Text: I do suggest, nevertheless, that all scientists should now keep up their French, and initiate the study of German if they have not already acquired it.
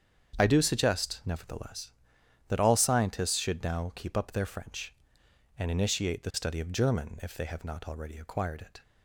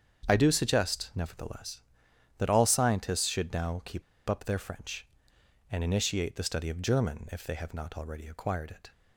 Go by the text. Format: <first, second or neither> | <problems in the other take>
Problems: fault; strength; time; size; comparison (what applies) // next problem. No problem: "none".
first | starts louder than the rest; strong; until 1.2 s; 7.5 dB; strong in the first // pauses between "keep" and "up"; slight; at 4.0 s; 0.25 s long